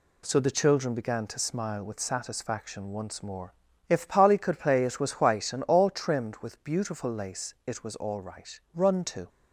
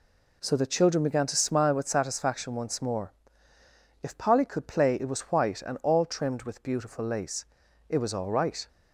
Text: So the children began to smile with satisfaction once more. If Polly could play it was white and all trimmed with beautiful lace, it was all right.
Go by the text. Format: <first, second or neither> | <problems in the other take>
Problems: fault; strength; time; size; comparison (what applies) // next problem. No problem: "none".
second | goes on to say "Run to"; from 8.7 s on; 0.56 s long